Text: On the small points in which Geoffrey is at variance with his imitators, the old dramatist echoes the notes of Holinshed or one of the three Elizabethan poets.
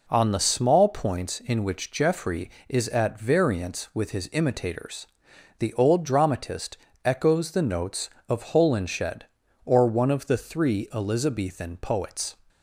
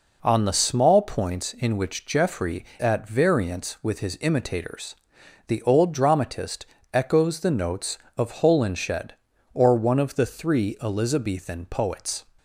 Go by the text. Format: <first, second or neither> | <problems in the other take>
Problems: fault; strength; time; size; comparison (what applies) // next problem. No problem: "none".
first | skips "is"; at 2.7 s // pauses between "dramatist" and "echoes"; slight; at 6.6 s; 0.28 s long; slight in the first